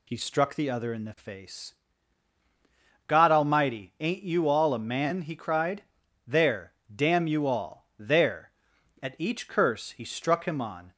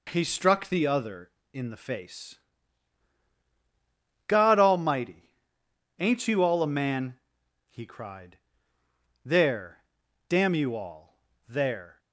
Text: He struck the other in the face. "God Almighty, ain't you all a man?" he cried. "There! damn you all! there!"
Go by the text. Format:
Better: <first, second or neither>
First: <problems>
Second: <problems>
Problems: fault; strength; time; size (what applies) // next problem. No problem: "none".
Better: second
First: goes on to say "At each curse he struck him on"; strong; from 9.0 s on; 1.9 s long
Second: none